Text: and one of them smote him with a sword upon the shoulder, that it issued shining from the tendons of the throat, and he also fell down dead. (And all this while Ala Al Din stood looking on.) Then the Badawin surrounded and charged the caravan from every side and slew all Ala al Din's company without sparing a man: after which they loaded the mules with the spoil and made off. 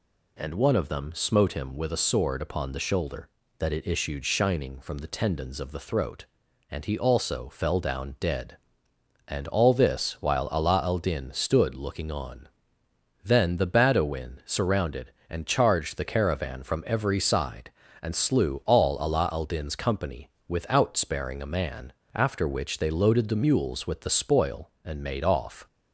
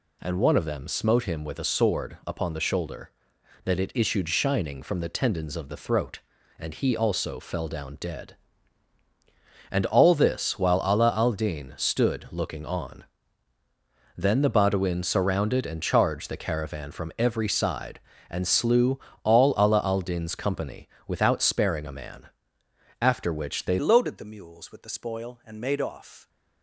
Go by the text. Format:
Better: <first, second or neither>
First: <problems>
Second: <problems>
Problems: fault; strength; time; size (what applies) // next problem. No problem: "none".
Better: first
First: pauses between "company" and "without"; slight; at 20.2 s; 0.18 s long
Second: pauses between "slew" and "all"; slight; at 18.9 s; 0.24 s long // pauses between "company" and "without"; slight; at 20.8 s; 0.18 s long // changes voice at "loaded"; from 23.7 s on; 2.5 s long